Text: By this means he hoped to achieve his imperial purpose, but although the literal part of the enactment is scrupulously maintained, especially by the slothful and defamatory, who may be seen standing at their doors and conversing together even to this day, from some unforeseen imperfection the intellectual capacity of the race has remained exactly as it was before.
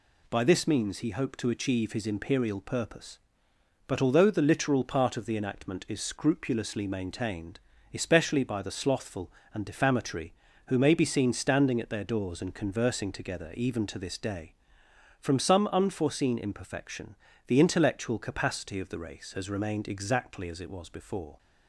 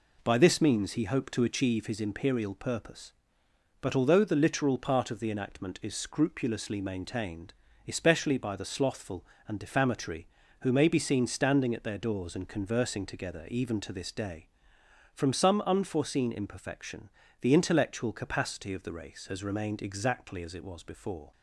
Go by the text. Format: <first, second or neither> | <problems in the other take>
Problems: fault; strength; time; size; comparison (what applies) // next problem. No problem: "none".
first | starts louder than the rest; slight; until 1.8 s; 3.5 dB // pauses between "imperfection" and "the"; slight; at 17.0 s; 0.32 s long; slight in the first